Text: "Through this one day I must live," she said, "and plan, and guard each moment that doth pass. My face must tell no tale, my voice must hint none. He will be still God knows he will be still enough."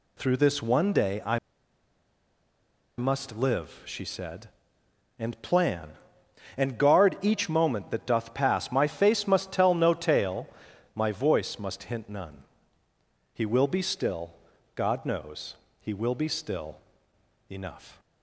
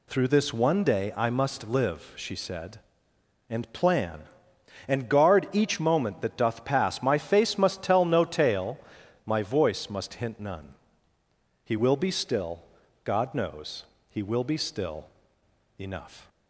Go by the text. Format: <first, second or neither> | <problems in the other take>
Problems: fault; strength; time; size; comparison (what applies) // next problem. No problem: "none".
second | pauses between "I" and "must"; strong; at 1.3 s; 1.6 s long // pauses between "still" and "God"; at 14.3 s; 0.40 s long; also in the second // pauses between "knows" and "he"; slight; at 15.5 s; 0.24 s long; slight in the second // pauses between "still" and "enough"; noticeable; at 16.7 s; 0.72 s long; noticeable in the second